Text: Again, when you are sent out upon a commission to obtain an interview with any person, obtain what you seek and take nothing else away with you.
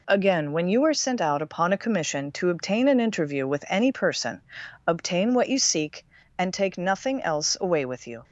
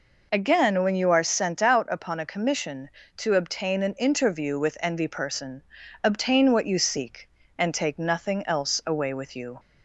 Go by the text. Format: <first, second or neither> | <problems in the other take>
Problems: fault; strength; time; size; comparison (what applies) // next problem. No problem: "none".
first | says "envy" for "any"; at 4.7 s